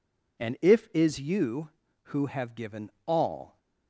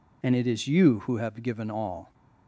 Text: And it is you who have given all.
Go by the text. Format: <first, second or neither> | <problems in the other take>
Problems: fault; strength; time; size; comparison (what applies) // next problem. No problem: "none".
second | says "if" for "it"; at 0.6 s // pauses between "given" and "all"; slight; at 2.8 s; 0.16 s long